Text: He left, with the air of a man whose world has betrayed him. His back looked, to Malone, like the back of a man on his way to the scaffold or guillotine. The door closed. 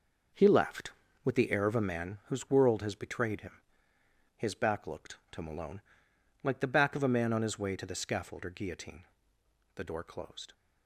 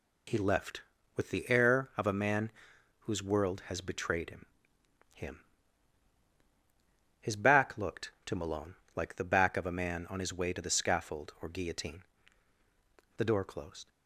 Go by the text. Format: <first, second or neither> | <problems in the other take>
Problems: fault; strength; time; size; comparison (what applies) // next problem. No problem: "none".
first | pauses between "man" and "whose"; noticeable; at 2.5 s; 0.50 s long // says "him" twice; at 5.1 s